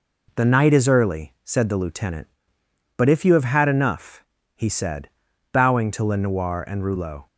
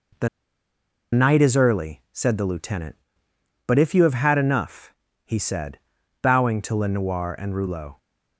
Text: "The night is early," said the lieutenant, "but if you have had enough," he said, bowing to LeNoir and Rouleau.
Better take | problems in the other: first | pauses between "The" and "night"; noticeable; at 0.2 s; 0.85 s long

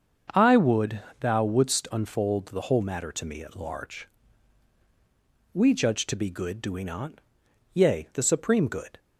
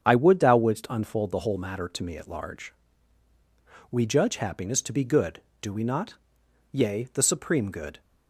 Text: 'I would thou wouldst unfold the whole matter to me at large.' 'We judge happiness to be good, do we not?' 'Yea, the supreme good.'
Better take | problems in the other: second | starts louder than the rest; until 1.5 s; 6.5 dB; strong in the second // pauses between "would" and "thou"; slight; at 1.0 s; 0.20 s long // skips "happiness"; at 6.0 s

